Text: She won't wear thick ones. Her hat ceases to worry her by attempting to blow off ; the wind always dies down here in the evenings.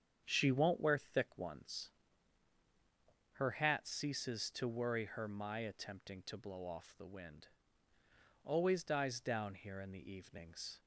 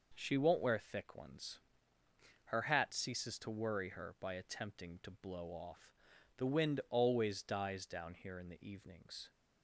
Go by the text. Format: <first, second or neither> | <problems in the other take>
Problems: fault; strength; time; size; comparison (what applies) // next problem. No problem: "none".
second | starts louder than the rest; strong; until 1.2 s; 8 dB // says "my" for "by"; at 5.2 s // pauses between "wind" and "always"; noticeable; at 7.4 s; 0.94 s long